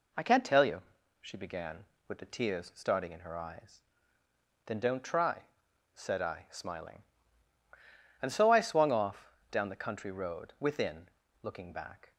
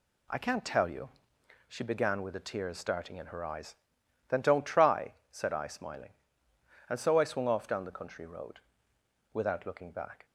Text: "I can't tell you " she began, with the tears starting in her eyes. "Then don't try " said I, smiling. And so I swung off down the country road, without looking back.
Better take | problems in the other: second | pauses between "off" and "down"; slight; at 9.3 s; 0.18 s long // says "within" for "without"; at 10.5 s

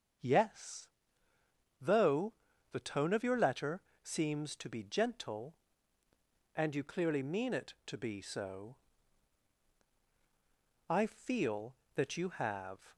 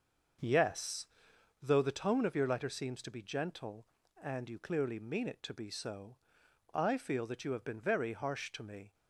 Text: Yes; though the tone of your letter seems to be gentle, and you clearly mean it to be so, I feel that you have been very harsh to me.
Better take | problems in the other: second | starts louder than the rest; strong; until 2.1 s; 7 dB; also in the second // pauses between "though" and "the"; at 2.3 s; 0.38 s long // pauses between "letter" and "seems"; slight; at 3.8 s; 0.22 s long // stops before "been very harsh to me"; at 12.9 s

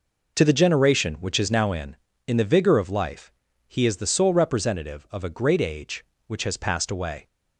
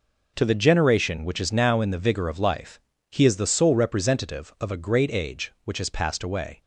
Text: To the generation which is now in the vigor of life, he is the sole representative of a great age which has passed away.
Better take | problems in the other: second | says "in" twice; at 2.2 s

